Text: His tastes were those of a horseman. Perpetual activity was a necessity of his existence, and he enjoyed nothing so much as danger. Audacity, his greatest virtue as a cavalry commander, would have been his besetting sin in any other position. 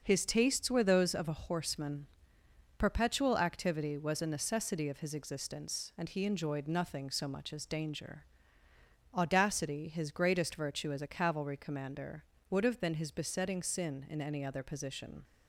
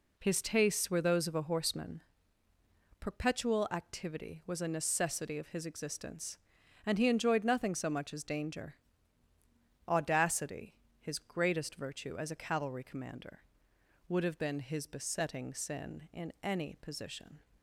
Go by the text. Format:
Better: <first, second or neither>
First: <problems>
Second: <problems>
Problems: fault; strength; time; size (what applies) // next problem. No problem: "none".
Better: first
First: none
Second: skips "other"; at 16.7 s